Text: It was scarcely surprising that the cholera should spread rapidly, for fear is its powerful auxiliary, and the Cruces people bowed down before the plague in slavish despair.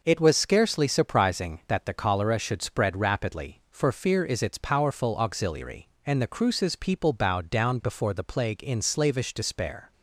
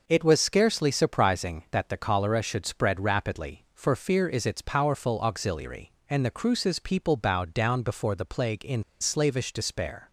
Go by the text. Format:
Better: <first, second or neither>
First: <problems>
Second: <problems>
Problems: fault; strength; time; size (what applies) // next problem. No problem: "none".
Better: first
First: none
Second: pauses between "in" and "slavish"; slight; at 8.8 s; 0.17 s long